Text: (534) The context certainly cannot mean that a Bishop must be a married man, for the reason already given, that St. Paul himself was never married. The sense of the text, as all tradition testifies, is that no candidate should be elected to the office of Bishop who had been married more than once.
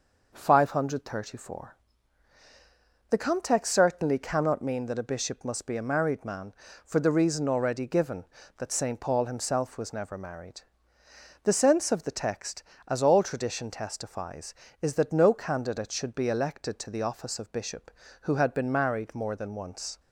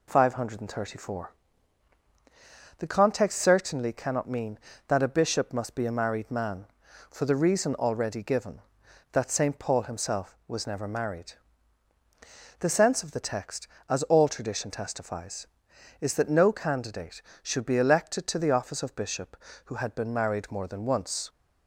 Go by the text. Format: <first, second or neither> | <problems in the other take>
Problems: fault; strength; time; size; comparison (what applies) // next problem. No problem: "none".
neither | none